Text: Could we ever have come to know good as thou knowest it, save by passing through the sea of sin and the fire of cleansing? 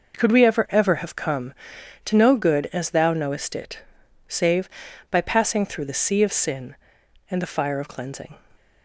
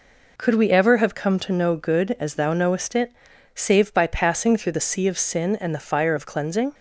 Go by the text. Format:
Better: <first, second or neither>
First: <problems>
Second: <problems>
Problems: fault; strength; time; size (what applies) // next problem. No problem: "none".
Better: second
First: says "ever" twice; at 0.7 s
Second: none